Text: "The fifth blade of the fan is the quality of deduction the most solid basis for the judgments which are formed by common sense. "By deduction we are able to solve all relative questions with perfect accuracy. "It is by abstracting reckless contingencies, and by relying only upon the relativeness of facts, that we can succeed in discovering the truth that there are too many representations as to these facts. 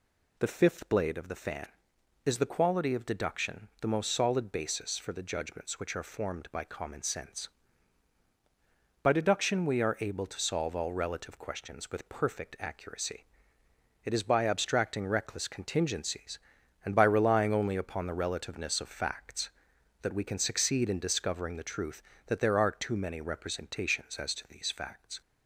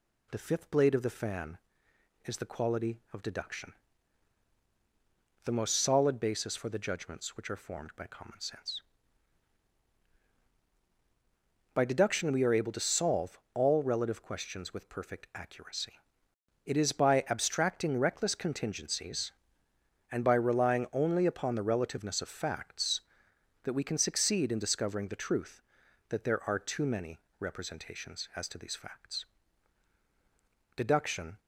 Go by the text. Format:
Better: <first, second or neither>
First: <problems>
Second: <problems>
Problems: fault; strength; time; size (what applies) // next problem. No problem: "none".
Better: first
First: none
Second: pauses between "deduction" and "the"; strong; at 3.7 s; 1.7 s long // pauses between "solve" and "all"; slight; at 13.3 s; 0.16 s long // pauses between "many" and "representations"; slight; at 27.1 s; 0.22 s long // goes on to say "Deduction"; noticeable; from 30.7 s on; 0.64 s long